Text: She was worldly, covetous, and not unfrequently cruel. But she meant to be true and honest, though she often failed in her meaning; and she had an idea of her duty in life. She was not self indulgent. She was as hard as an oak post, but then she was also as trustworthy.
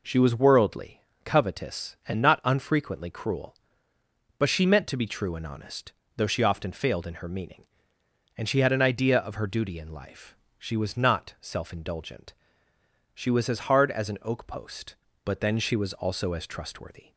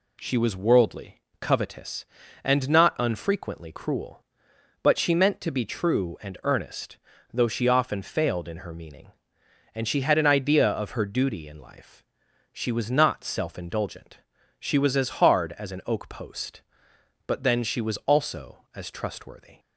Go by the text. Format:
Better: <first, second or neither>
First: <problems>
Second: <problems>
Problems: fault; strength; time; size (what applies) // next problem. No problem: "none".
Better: first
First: none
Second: says "earnest" for "honest"; at 6.4 s